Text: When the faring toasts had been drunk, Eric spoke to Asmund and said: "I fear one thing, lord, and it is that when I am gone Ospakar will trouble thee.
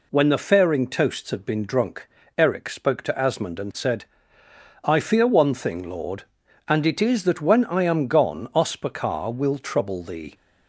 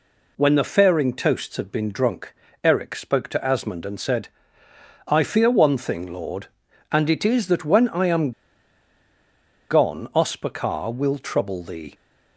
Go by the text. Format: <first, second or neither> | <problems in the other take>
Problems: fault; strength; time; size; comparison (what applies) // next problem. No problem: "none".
first | pauses between "am" and "gone"; strong; at 8.3 s; 1.3 s long